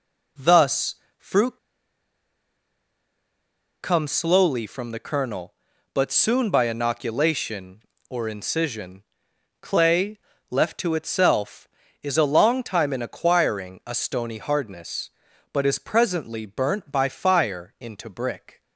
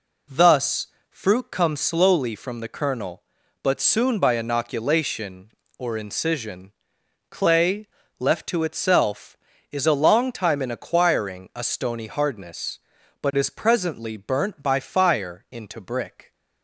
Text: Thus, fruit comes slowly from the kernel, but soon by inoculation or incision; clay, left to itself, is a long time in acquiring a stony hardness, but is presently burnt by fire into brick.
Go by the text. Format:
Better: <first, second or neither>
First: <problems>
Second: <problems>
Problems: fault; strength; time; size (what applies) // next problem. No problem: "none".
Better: second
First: pauses between "fruit" and "comes"; strong; at 1.5 s; 2.2 s long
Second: none